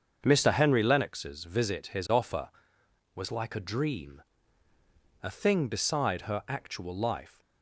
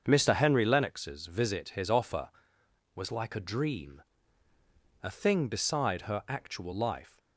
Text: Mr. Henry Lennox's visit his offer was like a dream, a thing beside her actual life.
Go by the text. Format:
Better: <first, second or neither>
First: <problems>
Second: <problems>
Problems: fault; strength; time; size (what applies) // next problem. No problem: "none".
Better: neither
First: starts louder than the rest; until 1.2 s; 7 dB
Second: starts louder than the rest; until 1.0 s; 7 dB